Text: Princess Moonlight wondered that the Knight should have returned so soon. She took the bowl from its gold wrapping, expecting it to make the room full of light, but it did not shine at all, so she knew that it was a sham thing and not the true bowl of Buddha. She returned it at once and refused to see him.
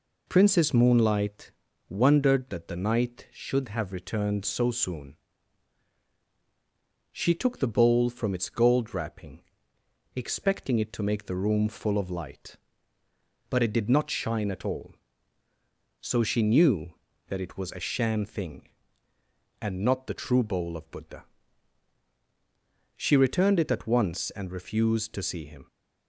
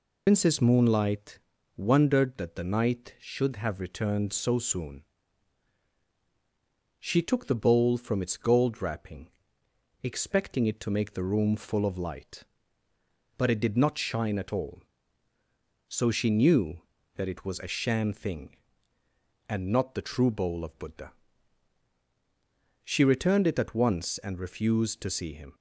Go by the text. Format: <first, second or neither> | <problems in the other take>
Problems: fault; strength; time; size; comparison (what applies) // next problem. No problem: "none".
first | loses the start of "Princess"; at 0.2 s; 105 ms // pauses between "Moonlight" and "wondered"; slight; at 1.4 s; 0.36 s long; slight in the first